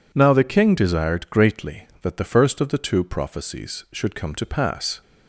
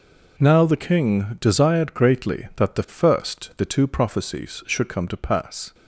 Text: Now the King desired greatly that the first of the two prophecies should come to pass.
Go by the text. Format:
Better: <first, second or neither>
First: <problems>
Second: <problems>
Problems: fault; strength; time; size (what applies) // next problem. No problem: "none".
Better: first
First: none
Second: skips "of"; at 3.5 s